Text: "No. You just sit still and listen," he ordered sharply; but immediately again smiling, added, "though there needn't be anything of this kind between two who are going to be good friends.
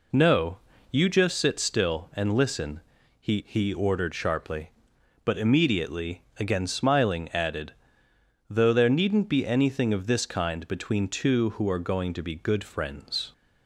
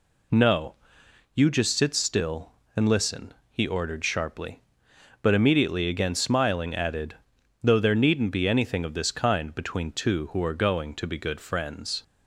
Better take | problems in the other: second | says "he" twice; at 3.4 s

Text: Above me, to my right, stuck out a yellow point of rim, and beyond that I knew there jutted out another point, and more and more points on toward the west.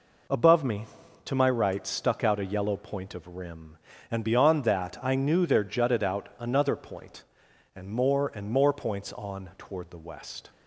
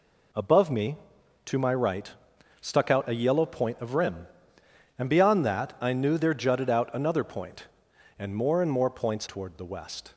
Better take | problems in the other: first | skips "on"; at 9.2 s

